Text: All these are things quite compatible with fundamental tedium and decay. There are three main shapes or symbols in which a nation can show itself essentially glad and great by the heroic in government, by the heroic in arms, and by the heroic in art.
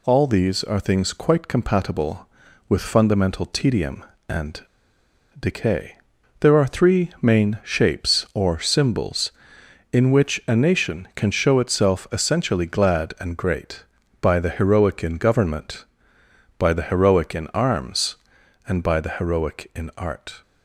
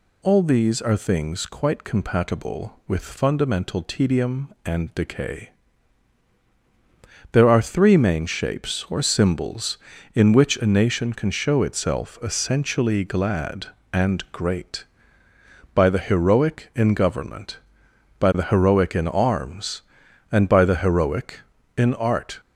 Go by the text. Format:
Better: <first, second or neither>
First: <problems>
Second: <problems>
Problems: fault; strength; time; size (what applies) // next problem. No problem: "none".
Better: second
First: pauses between "and" and "decay"; noticeable; at 4.6 s; 0.77 s long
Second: none